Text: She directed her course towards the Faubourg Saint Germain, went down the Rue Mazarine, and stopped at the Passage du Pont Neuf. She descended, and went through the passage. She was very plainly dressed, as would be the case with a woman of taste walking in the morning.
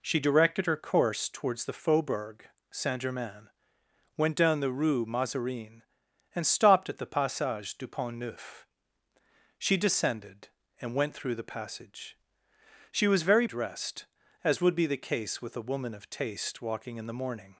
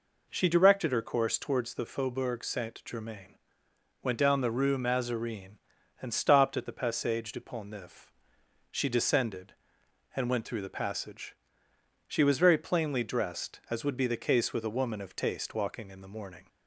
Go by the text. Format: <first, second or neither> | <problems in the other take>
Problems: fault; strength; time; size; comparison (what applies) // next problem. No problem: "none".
second | pauses between "Faubourg" and "Saint"; slight; at 2.4 s; 0.24 s long // skips "plainly"; at 13.4 s